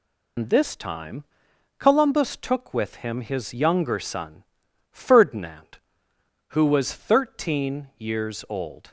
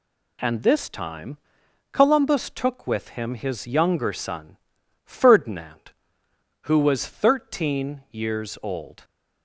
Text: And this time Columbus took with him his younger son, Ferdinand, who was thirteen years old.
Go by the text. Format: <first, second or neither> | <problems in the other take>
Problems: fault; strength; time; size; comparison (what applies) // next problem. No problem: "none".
second | loses the start of "And"; at 0.3 s; 115 ms // pauses between "time" and "Columbus"; noticeable; at 1.2 s; 0.54 s long; noticeable in the second